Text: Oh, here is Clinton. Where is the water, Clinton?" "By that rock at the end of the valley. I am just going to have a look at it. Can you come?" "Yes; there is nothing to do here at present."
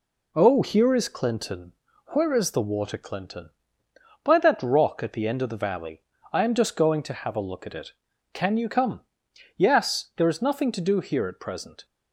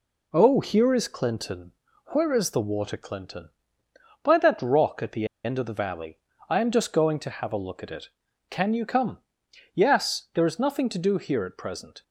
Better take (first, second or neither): first